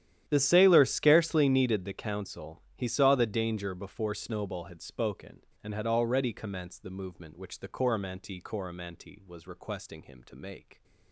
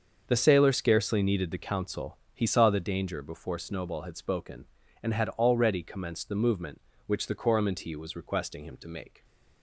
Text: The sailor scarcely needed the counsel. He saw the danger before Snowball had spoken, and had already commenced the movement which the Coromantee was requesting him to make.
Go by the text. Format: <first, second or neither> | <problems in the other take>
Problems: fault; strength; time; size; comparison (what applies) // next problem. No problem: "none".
second | starts louder than the rest; strong; until 1.2 s; 11 dB; also in the second // says "Coromantee" twice; at 8.3 s